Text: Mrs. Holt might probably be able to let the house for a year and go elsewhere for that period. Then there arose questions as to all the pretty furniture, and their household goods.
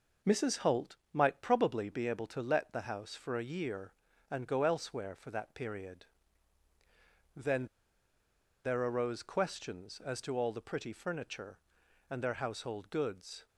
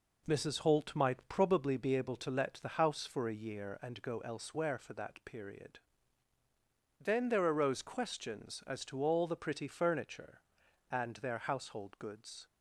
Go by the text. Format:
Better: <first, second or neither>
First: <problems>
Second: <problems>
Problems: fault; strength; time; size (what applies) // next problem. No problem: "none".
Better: second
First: pauses between "Holt" and "might"; slight; at 0.9 s; 0.18 s long // pauses between "Then" and "there"; at 7.6 s; 0.98 s long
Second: none